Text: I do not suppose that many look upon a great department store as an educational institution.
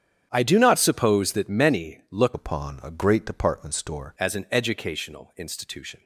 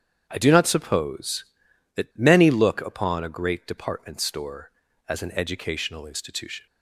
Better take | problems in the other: second | starts louder than the rest; strong; until 1.3 s; 9 dB; strong in the second // changes voice from "upon" to "store"; from 2.3 to 4.1 s; 1.8 s long

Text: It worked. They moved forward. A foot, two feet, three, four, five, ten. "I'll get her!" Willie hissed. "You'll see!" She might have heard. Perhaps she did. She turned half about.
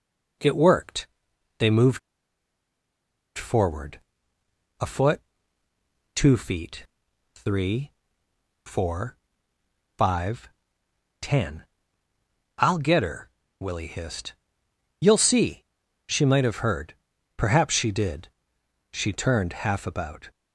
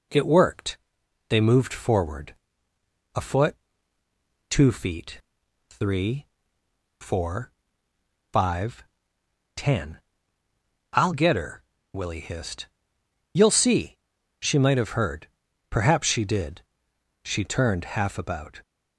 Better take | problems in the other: second | pauses between "moved" and "forward"; strong; at 1.9 s; 1.3 s long

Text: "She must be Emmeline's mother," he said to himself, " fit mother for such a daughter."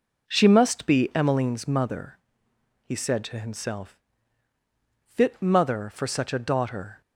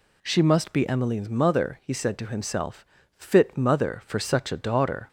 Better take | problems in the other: neither | none

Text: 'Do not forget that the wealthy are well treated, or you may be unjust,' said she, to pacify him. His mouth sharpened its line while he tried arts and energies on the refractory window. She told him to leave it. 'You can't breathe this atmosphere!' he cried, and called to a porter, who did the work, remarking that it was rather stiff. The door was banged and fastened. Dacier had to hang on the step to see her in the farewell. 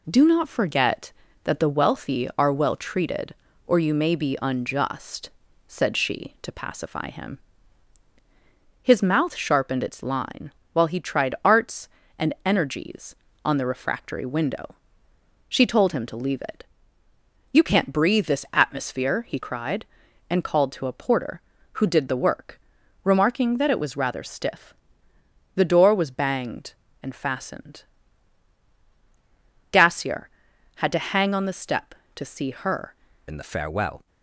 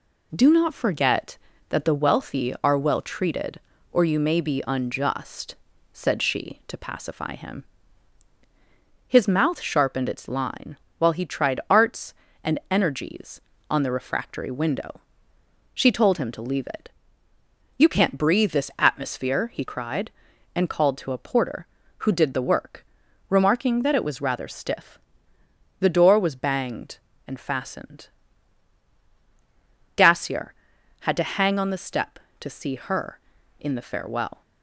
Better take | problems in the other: second | pauses between "line" and "while"; slight; at 10.5 s; 0.22 s long; slight in the second // changes voice at "in"; from 33.2 s on; 0.8 s long

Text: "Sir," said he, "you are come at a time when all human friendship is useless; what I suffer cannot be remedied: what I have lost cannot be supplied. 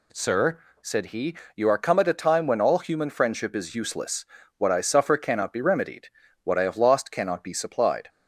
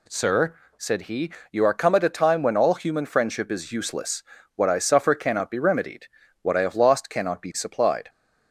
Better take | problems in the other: neither | none

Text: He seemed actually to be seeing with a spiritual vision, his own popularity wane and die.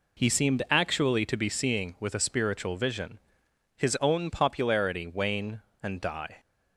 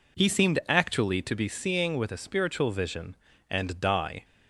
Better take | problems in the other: first | skips "his own popularity wane"; at 3.3 s

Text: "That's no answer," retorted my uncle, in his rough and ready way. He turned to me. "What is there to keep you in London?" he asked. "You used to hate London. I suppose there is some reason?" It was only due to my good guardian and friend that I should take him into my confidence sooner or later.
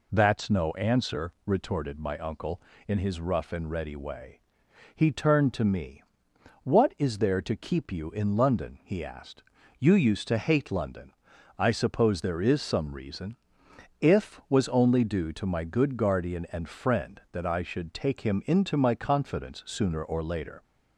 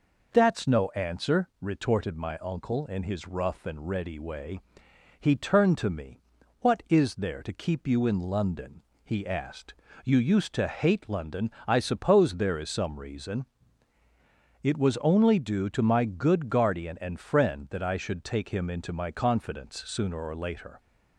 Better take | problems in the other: second | says "If" for "It"; at 14.0 s

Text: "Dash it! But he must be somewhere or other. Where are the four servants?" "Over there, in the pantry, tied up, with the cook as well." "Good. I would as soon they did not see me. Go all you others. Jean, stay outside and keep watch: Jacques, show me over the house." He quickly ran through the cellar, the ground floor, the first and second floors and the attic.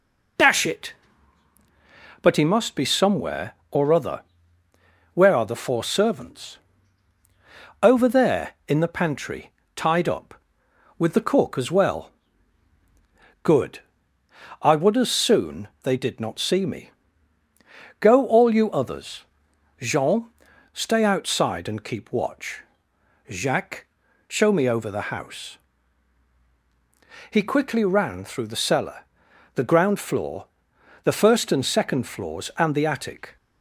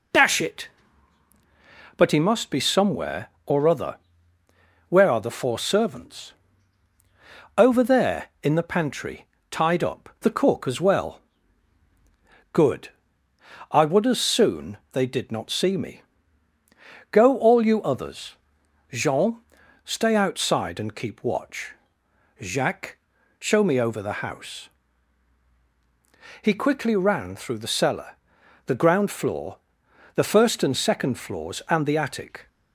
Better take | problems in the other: first | skips "with"; at 10.1 s

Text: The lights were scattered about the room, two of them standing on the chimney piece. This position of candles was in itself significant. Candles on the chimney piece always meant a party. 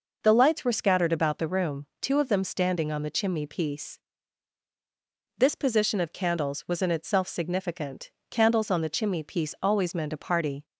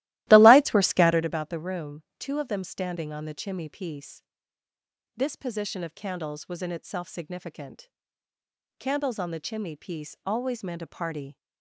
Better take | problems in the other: first | starts louder than the rest; strong; until 1.3 s; 16.5 dB

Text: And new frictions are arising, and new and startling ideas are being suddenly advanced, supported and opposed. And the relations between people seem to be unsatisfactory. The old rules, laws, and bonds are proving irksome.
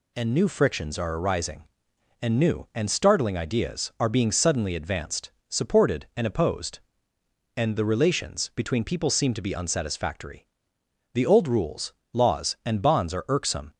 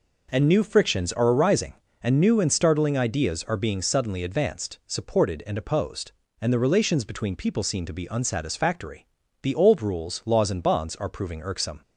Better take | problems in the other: second | skips "proving"; at 13.2 s

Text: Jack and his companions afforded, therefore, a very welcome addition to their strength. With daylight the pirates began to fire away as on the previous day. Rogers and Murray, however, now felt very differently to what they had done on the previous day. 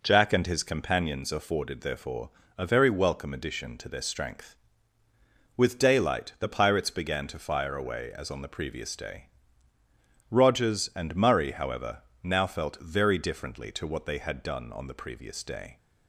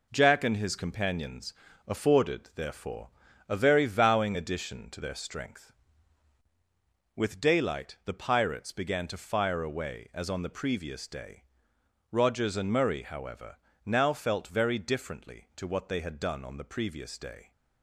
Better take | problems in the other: first | pauses between "companions" and "afforded"; slight; at 1.5 s; 0.34 s long // says "vowing" for "welcome"; at 3.8 s

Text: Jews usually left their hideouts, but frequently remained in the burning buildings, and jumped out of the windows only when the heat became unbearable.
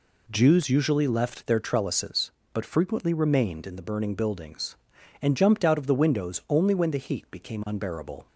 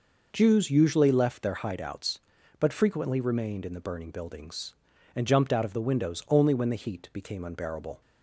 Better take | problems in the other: second | says "trellises" for "hideouts"; at 1.6 s

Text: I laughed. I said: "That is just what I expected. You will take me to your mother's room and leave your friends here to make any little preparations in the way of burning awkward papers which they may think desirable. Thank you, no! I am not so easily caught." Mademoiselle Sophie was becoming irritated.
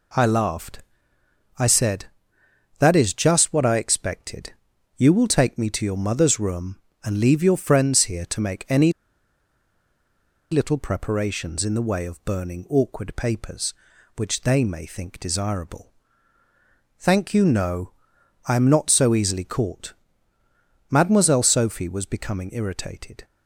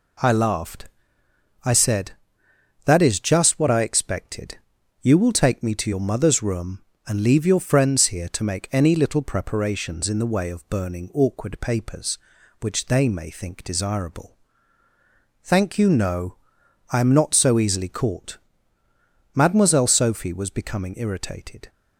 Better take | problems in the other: second | pauses between "any" and "little"; strong; at 8.9 s; 1.5 s long

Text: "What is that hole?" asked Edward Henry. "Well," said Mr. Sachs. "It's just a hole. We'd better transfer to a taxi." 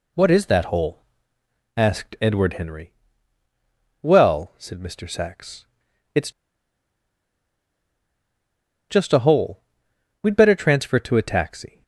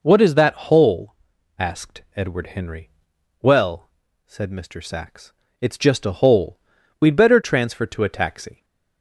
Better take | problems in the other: second | pauses between "It's" and "just"; strong; at 6.2 s; 2.5 s long

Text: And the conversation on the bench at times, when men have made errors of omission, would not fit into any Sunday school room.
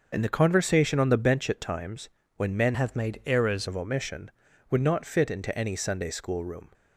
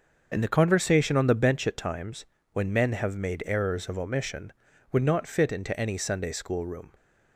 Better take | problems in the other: second | starts louder than the rest; until 1.1 s; 6 dB; also in the second // changes voice from "have" to "errors"; from 2.7 to 3.6 s; 0.9 s long

